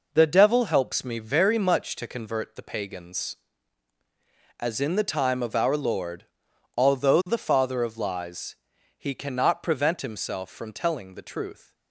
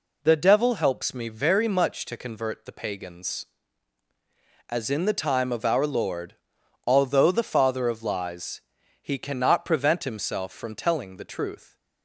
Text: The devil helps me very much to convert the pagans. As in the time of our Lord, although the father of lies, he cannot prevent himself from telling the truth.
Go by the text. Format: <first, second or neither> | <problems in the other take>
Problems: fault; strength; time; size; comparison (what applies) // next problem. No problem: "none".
second | gets quieter; throughout; 6.5 dB